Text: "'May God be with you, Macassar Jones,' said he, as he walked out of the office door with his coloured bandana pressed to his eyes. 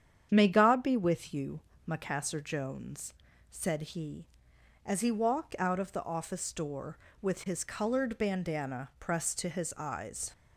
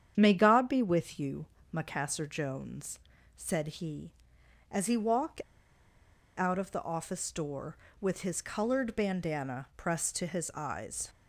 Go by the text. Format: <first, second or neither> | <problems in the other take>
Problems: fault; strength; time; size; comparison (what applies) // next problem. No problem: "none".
first | starts louder than the rest; strong; until 1.1 s; 8.5 dB; strong in the first // pauses between "walked" and "out"; noticeable; at 5.4 s; 0.95 s long